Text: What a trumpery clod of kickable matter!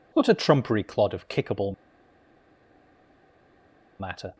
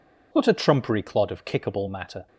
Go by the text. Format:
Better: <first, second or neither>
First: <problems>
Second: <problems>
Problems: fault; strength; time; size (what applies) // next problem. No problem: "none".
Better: second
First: pauses between "kickable" and "matter"; strong; at 1.7 s; 2.2 s long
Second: none